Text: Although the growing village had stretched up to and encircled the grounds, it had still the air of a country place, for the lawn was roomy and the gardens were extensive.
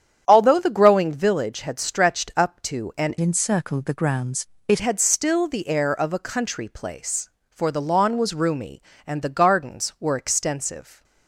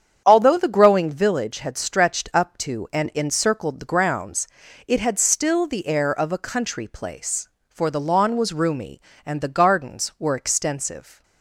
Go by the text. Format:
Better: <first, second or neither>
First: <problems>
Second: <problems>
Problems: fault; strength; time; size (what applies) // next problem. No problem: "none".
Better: second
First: starts louder than the rest; strong; until 1.2 s; 9 dB // changes voice from "encircled" to "it"; from 3.2 to 4.8 s; 1.6 s long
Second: starts louder than the rest; strong; until 1.2 s; 8 dB